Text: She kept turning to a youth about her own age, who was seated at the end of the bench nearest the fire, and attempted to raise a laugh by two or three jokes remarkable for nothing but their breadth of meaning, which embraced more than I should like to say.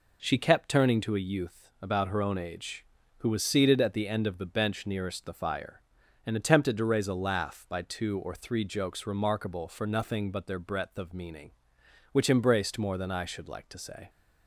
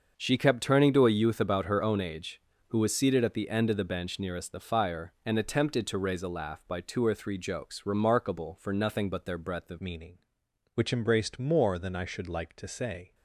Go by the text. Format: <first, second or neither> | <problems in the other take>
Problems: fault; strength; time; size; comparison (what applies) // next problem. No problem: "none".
first | starts louder than the rest; until 1.1 s; 6.5 dB // changes voice at "meaning"; from 9.8 s on; 3.3 s long